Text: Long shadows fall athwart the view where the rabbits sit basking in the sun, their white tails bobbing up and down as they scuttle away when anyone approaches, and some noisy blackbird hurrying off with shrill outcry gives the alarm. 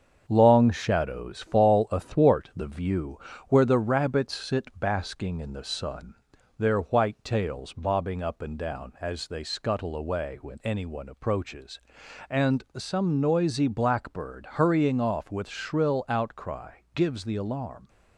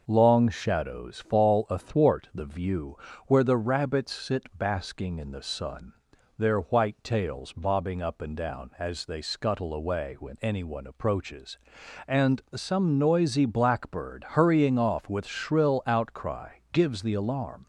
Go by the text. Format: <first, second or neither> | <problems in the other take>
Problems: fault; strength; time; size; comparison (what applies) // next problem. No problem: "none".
second | gets quieter; noticeable; throughout; 4 dB // pauses between "view" and "where"; slight; at 3.1 s; 0.30 s long; slight in the second